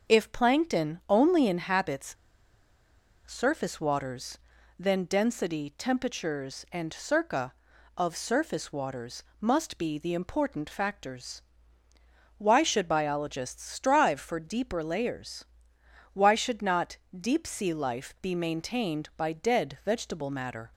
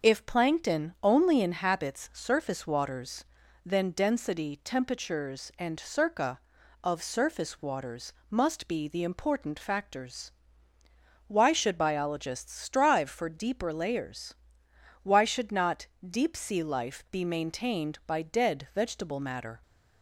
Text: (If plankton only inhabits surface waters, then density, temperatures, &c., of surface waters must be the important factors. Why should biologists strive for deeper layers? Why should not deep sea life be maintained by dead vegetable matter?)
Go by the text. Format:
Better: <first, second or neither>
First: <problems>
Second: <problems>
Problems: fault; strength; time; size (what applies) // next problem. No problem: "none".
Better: second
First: starts louder than the rest; until 1.1 s; 6 dB // pauses between "inhabits" and "surface"; at 2.1 s; 1.1 s long // pauses between "waters" and "must"; slight; at 9.2 s; 0.16 s long // pauses between "not" and "deep"; slight; at 16.9 s; 0.22 s long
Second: starts louder than the rest; until 1.1 s; 6 dB // pauses between "waters" and "must"; slight; at 8.1 s; 0.16 s long // pauses between "not" and "deep"; slight; at 15.8 s; 0.22 s long